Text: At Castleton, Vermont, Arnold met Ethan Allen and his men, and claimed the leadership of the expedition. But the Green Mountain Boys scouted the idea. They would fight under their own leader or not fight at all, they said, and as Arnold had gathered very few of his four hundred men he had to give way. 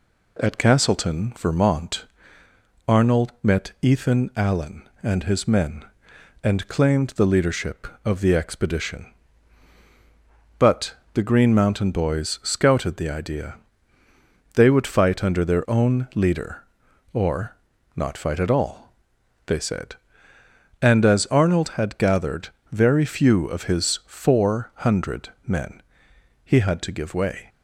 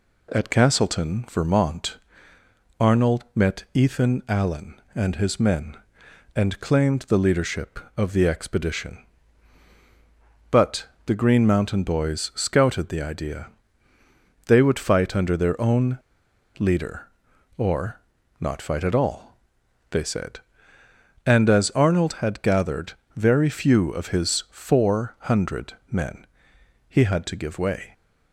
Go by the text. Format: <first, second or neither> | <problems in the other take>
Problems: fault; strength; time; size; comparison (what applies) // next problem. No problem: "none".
first | pauses between "But" and "the"; slight; at 10.8 s; 0.20 s long; slight in the first // pauses between "own" and "leader"; noticeable; at 15.9 s; 0.61 s long // pauses between "or" and "not"; at 18.0 s; 0.40 s long; also in the first // pauses between "gathered" and "very"; slight; at 22.9 s; 0.22 s long; slight in the first // pauses between "hundred" and "men"; slight; at 25.7 s; 0.16 s long; slight in the first // pauses between "men" and "he"; noticeable; at 26.2 s; 0.64 s long; noticeable in the first